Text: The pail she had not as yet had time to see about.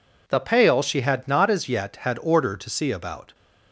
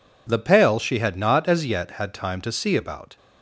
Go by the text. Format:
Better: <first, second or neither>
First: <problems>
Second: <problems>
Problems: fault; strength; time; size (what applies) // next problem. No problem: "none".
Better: second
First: says "order" for "time"; at 2.2 s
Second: none